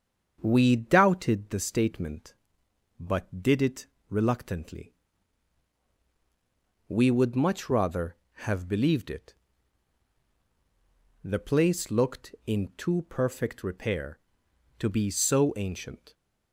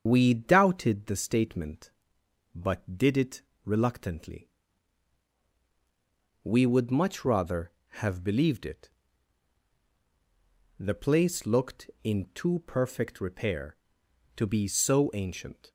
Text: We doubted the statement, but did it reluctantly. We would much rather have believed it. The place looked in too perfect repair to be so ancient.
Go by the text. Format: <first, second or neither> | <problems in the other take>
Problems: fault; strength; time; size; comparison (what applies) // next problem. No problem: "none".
first | loses the start of "We"; at 0.0 s; 85 ms // starts louder than the rest; strong; until 1.0 s; 7.5 dB; strong in the first // pauses between "it" and "reluctantly"; slight; at 3.4 s; 0.22 s long; slight in the first